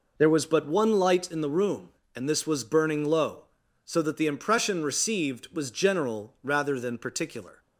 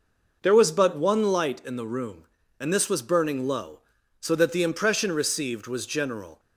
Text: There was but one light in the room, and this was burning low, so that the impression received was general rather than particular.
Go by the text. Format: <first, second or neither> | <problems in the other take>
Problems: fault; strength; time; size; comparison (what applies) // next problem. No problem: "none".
first | stops before "rather than particular"; at 6.3 s